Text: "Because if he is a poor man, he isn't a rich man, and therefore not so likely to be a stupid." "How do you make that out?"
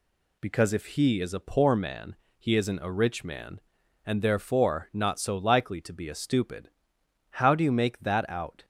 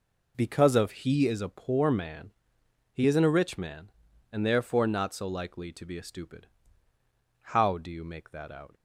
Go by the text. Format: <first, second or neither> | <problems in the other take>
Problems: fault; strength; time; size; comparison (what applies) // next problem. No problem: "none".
first | says "of" for "if"; at 0.7 s